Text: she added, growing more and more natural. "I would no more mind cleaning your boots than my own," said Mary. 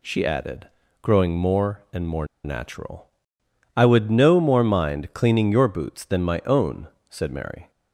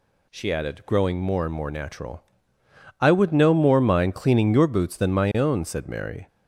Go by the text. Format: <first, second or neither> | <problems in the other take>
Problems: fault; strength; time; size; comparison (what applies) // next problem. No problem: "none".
second | pauses between "more" and "natural"; slight; at 2.2 s; 0.17 s long